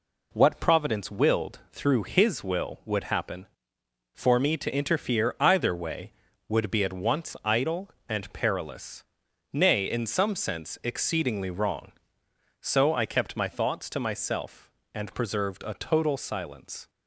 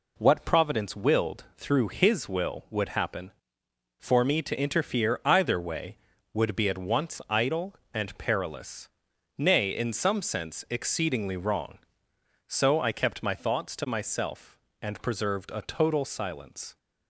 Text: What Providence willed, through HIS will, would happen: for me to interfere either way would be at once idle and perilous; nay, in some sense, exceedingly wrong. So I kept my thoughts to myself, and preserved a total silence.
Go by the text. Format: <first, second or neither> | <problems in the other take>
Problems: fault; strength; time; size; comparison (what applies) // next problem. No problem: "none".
neither | none